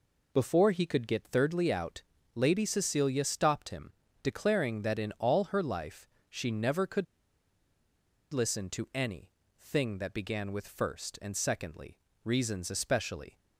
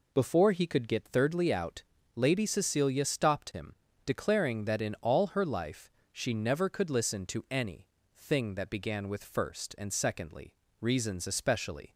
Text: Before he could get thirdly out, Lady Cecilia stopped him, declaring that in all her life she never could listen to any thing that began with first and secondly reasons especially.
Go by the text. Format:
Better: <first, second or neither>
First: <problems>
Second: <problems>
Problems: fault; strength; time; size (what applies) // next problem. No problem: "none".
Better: second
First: pauses between "life" and "she"; slight; at 6.0 s; 0.22 s long // pauses between "could" and "listen"; strong; at 7.0 s; 1.2 s long // pauses between "any" and "thing"; slight; at 9.3 s; 0.30 s long // pauses between "secondly" and "reasons"; slight; at 11.9 s; 0.28 s long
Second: pauses between "life" and "she"; slight; at 5.8 s; 0.22 s long // pauses between "any" and "thing"; slight; at 7.8 s; 0.30 s long // pauses between "secondly" and "reasons"; slight; at 10.5 s; 0.28 s long